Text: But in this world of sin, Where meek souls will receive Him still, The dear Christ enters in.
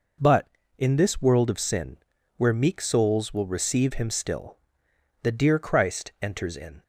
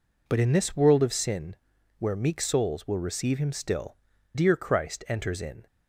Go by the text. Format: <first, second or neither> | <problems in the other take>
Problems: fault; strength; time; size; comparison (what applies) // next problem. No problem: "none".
first | skips "The"; at 4.1 s